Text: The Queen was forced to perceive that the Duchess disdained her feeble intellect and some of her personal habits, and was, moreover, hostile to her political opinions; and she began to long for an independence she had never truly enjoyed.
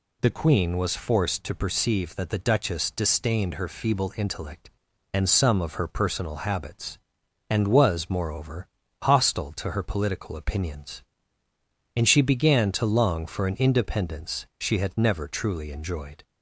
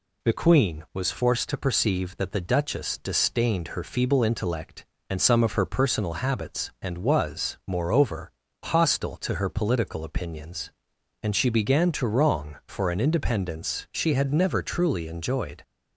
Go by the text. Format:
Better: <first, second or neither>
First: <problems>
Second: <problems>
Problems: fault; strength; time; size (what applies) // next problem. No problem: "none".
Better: first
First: none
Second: says "wrong" for "long"; at 12.0 s